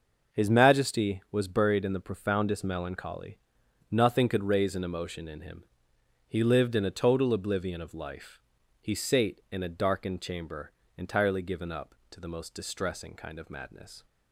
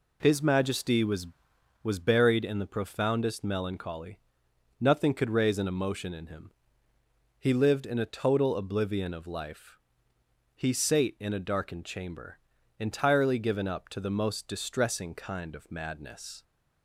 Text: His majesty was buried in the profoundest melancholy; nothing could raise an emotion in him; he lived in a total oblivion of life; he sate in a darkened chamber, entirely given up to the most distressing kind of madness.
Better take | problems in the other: first | says "was" twice; at 1.8 s

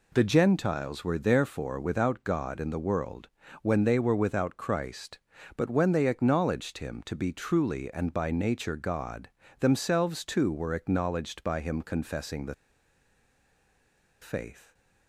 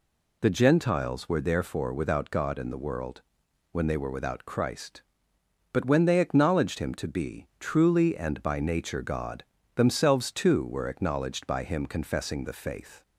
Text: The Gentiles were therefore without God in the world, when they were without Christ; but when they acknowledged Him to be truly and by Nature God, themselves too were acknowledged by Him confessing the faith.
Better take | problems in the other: second | pauses between "the" and "faith"; strong; at 12.5 s; 1.6 s long

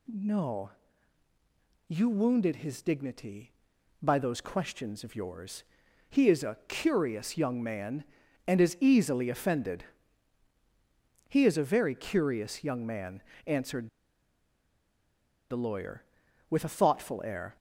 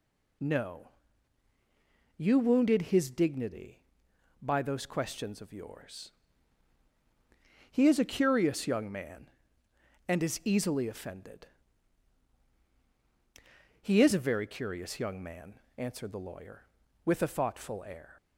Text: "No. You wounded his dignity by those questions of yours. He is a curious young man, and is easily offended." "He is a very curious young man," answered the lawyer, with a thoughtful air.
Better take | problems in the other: second | pauses between "answered" and "the"; strong; at 13.8 s; 1.6 s long

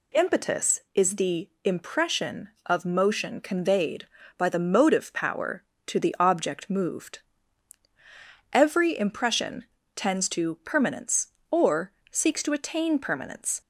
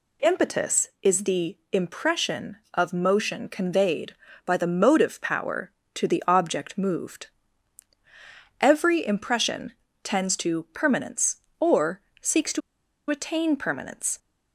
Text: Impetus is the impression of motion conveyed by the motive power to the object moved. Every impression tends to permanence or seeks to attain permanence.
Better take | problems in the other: first | pauses between "the" and "impression"; slight; at 1.5 s; 0.16 s long; slight in the first // pauses between "impression" and "tends"; slight; at 9.7 s; 0.30 s long; slight in the first // pauses between "or" and "seeks"; slight; at 12.0 s; 0.20 s long; slight in the first // pauses between "to" and "attain"; noticeable; at 12.6 s; 0.49 s long

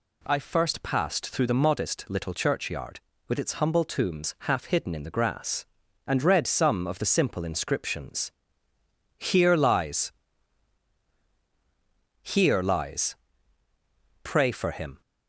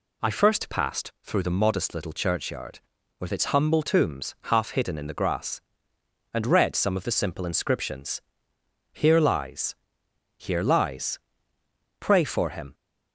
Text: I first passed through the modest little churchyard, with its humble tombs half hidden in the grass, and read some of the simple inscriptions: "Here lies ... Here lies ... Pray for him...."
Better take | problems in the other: neither | none

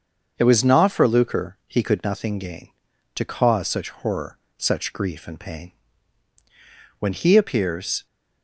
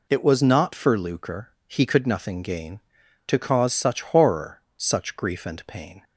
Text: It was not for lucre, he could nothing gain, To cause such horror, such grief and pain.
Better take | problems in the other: second | starts louder than the rest; until 1.3 s; 7 dB // goes on to say "When he appears"; noticeable; from 6.9 s on; 1.0 s long

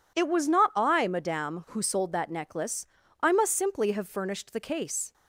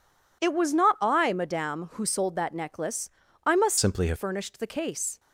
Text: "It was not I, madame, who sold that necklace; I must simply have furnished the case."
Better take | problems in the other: first | changes voice from "simply" to "have"; from 3.7 to 4.1 s; 0.4 s long

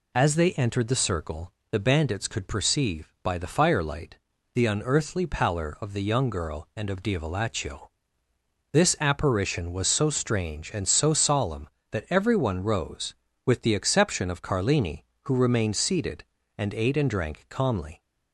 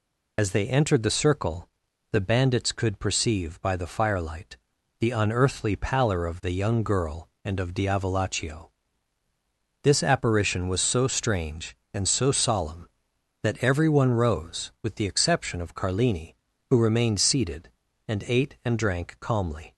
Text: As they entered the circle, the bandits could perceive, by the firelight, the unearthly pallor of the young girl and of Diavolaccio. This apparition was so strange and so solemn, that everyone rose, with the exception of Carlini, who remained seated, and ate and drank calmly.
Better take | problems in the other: first | loses the start of "As"; at 0.3 s; 55 ms

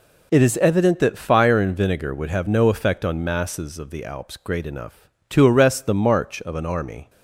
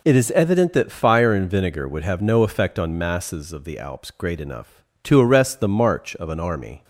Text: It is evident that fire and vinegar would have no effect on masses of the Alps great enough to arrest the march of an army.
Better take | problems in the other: neither | none

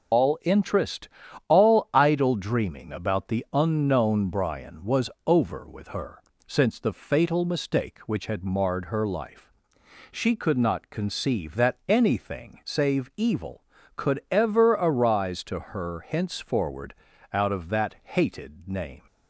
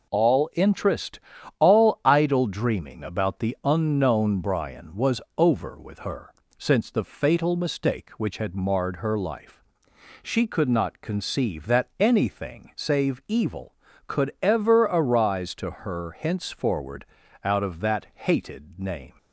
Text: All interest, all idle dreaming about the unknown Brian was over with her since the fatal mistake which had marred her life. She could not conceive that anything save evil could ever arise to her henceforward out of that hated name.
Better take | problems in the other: second | loses the start of "All"; at 0.1 s; 130 ms // pauses between "was" and "over"; slight; at 5.0 s; 0.16 s long; slight in the second // pauses between "her" and "since"; slight; at 6.2 s; 0.26 s long; slight in the second // pauses between "henceforward" and "out"; at 16.9 s; 0.40 s long; also in the second

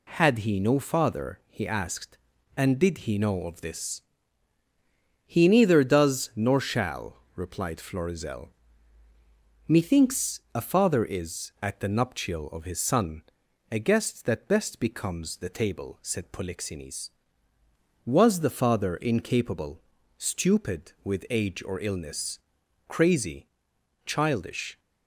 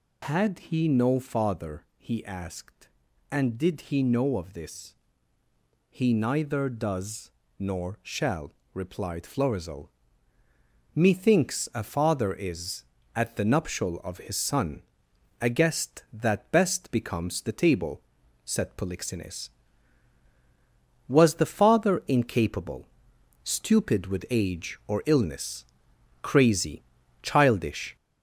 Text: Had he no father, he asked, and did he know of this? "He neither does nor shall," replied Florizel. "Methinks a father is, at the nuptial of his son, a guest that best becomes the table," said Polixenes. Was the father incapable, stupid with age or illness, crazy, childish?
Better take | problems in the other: first | gets louder; noticeable; throughout; 4.5 dB // pauses between "does" and "nor"; slight; at 7.2 s; 0.30 s long

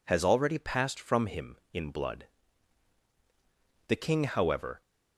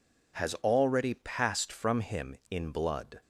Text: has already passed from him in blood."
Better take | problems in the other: second | goes on to say "The king however"; noticeable; from 3.8 s on; 0.94 s long

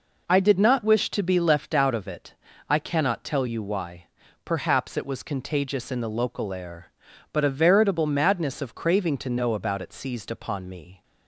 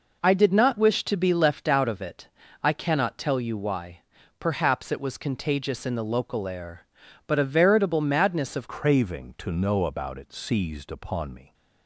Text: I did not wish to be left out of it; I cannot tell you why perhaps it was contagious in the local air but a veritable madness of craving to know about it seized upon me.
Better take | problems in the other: first | pauses between "why" and "perhaps"; slight; at 4.0 s; 0.36 s long; slight in the first // changes voice at "craving"; from 8.6 s on; 2.9 s long

